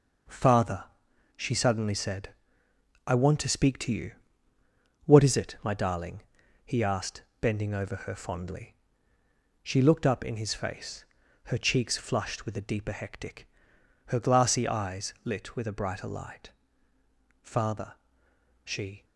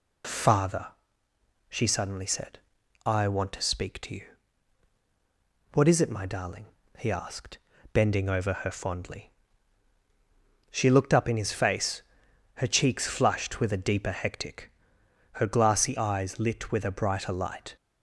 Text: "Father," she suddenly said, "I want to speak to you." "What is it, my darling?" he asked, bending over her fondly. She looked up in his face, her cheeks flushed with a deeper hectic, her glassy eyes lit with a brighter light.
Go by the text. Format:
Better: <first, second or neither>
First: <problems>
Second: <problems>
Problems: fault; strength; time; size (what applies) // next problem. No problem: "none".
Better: second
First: goes on to say "Father she"; from 17.4 s on; 1.6 s long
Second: none